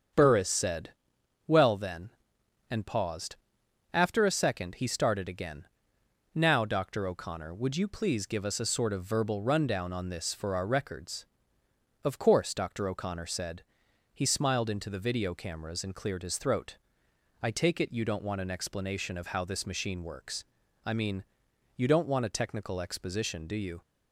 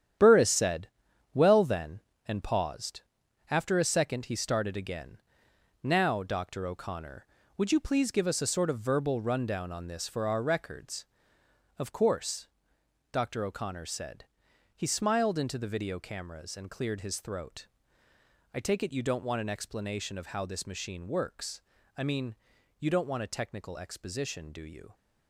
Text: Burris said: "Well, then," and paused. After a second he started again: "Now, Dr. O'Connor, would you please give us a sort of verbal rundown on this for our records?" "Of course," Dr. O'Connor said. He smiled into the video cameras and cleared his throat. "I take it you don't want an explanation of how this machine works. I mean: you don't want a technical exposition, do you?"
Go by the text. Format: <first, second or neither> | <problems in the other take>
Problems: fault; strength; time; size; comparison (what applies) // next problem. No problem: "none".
first | gets quieter; strong; throughout; 9 dB // starts louder than the rest; strong; until 1.6 s; 9.5 dB; strong in the first